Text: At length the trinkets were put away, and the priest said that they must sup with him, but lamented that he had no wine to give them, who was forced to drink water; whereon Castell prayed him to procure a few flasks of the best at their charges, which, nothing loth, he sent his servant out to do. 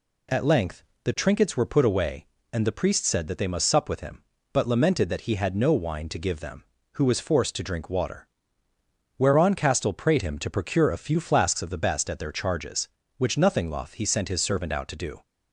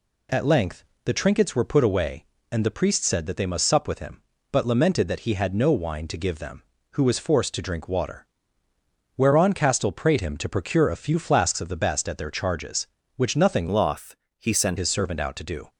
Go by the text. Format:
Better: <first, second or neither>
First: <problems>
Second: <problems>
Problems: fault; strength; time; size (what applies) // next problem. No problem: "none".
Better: first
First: pauses between "length" and "the"; slight; at 0.8 s; 0.20 s long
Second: pauses between "length" and "the"; slight; at 0.8 s; 0.20 s long // changes voice from "loth" to "sent"; from 13.6 to 14.7 s; 1.1 s long